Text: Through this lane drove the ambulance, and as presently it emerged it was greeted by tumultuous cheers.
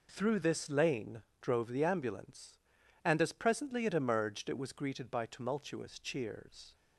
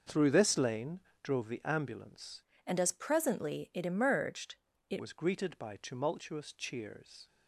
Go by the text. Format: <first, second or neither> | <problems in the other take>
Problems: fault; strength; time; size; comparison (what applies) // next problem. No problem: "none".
first | pauses between "lane" and "drove"; slight; at 1.0 s; 0.20 s long; slight in the first // changes voice from "and" to "it"; from 2.6 to 4.9 s; 2.3 s long // pauses between "emerged" and "it"; slight; at 4.5 s; 0.34 s long